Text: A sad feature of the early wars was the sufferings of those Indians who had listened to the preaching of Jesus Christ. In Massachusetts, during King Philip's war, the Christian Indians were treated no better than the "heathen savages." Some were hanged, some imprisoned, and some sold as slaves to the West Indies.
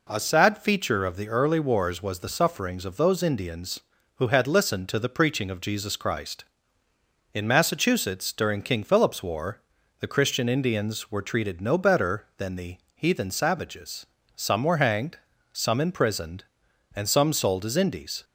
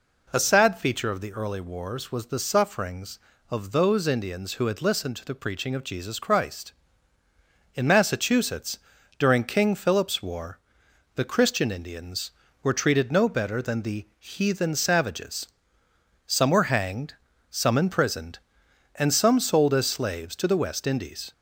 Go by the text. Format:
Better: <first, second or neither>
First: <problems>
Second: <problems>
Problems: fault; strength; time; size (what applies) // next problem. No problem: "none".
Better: second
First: pauses between "the" and "heathen"; slight; at 12.7 s; 0.16 s long // skips "slaves to the West"; at 17.7 s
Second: none